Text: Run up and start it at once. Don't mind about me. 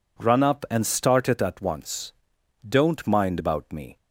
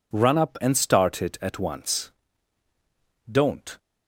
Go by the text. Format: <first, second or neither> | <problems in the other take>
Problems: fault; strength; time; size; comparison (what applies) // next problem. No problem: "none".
first | stops before "mind about me"; at 3.7 s